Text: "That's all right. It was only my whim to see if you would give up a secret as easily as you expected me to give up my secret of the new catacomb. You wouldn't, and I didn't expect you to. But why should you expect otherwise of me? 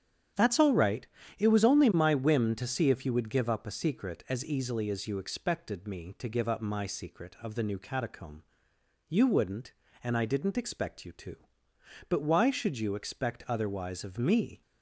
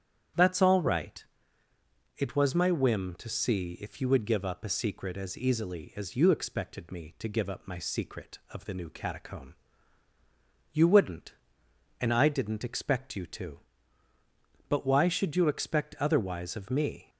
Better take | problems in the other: first | starts louder than the rest; strong; until 2.3 s; 9 dB; strong in the first // skips "only"; at 2.5 s

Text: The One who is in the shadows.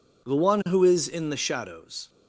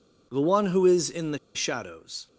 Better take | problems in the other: first | pauses between "the" and "shadows"; slight; at 1.3 s; 0.16 s long

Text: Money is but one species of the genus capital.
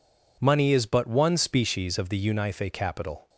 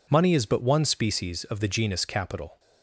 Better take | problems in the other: second | says "unife" for "genus"; at 2.2 s

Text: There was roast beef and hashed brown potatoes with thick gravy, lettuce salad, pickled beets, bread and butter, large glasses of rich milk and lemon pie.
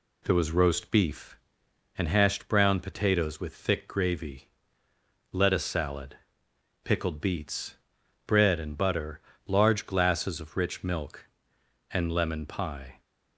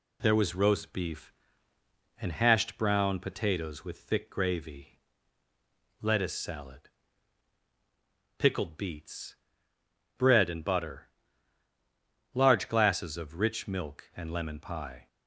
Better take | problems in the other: neither | none

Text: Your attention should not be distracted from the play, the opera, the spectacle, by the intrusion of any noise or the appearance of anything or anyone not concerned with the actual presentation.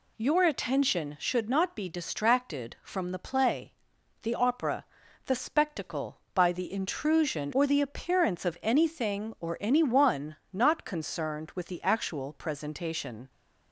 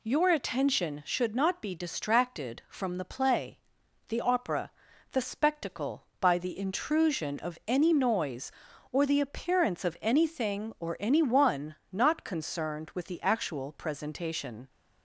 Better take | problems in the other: second | skips "of any noise"; at 7.5 s // pauses between "anyone" and "not"; slight; at 10.3 s; 0.16 s long; slight in the second

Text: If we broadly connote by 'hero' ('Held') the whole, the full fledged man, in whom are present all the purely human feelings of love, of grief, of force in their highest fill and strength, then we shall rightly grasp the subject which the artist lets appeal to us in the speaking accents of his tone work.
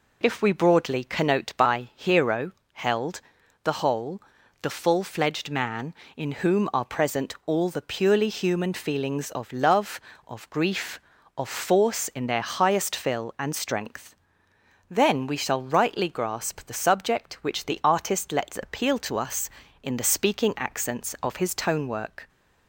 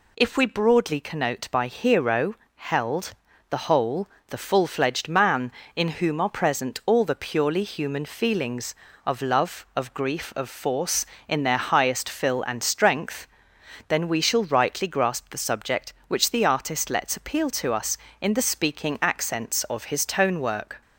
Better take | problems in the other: neither | none

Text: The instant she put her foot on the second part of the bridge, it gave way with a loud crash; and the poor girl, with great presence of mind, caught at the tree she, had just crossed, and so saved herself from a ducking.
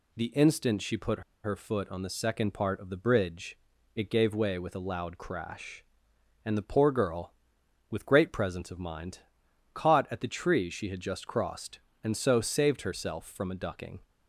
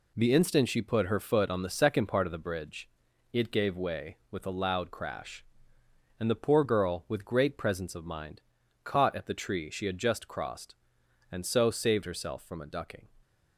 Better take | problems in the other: second | pauses between "put" and "her"; slight; at 1.2 s; 0.22 s long

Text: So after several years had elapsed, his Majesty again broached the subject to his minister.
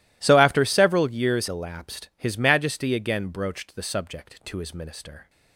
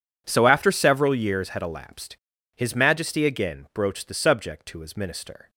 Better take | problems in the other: second | skips "had"; at 1.4 s

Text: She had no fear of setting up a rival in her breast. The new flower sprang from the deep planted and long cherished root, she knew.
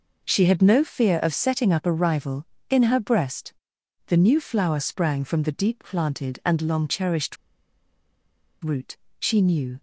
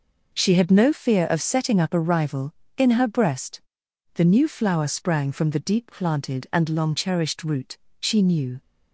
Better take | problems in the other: second | pauses between "cherished" and "root"; strong; at 7.3 s; 1.2 s long

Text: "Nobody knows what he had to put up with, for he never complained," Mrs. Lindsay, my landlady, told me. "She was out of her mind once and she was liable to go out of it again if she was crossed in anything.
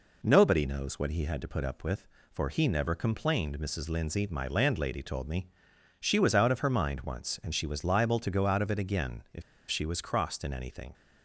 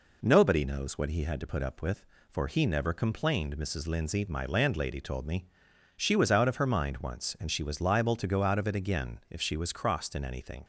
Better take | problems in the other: second | pauses between "if" and "she"; slight; at 9.4 s; 0.28 s long

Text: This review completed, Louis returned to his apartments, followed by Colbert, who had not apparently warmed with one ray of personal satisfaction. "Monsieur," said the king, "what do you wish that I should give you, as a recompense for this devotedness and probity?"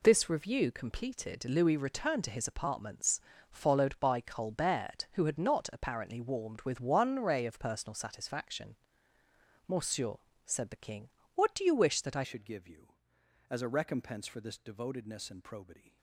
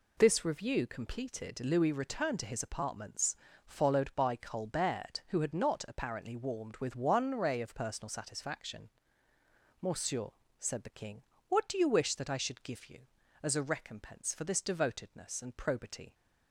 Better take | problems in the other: second | changes voice at "should"; from 12.2 s on; 3.7 s long

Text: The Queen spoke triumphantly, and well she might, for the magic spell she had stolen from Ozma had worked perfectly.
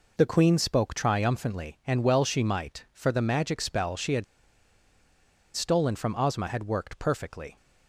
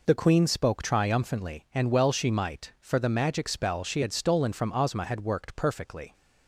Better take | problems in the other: second | pauses between "had" and "stolen"; strong; at 4.2 s; 1.2 s long

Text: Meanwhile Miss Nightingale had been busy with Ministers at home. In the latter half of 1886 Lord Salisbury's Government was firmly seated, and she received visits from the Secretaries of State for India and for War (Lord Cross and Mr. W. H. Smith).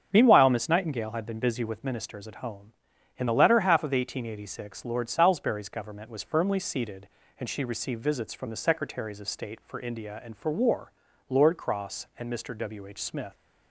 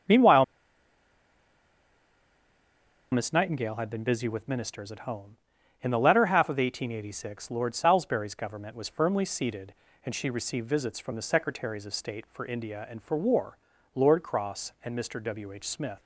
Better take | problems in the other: first | starts louder than the rest; strong; until 3.7 s; 7.5 dB; strong in the first // pauses between "Meanwhile" and "Miss"; strong; at 0.4 s; 2.6 s long

